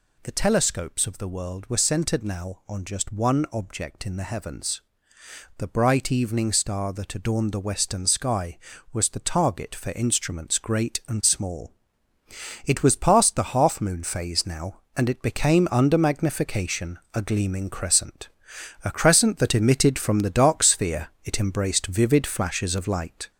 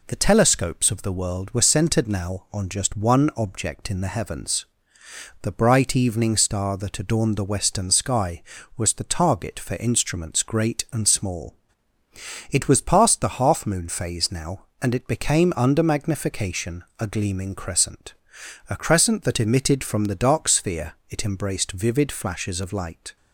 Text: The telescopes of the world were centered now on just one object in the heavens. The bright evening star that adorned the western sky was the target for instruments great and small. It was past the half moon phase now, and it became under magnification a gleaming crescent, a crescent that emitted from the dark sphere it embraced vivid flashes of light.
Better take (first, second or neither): second